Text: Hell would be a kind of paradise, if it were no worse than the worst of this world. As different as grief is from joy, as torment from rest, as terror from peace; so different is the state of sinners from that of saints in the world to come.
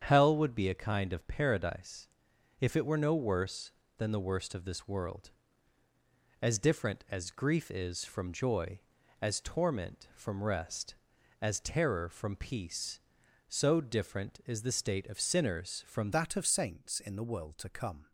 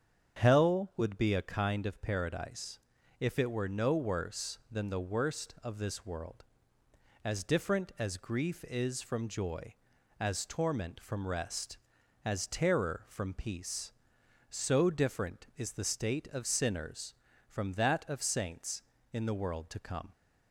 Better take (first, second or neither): second